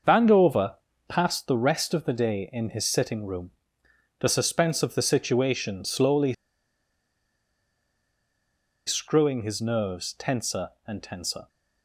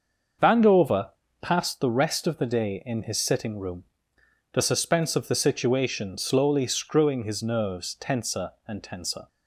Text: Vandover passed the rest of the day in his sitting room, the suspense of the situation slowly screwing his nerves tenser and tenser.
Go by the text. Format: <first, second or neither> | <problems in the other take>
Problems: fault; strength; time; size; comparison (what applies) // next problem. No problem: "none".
second | starts louder than the rest; until 1.3 s; 6.5 dB; also in the second // pauses between "Vandover" and "passed"; slight; at 0.7 s; 0.32 s long; slight in the second // pauses between "slowly" and "screwing"; strong; at 6.3 s; 2.5 s long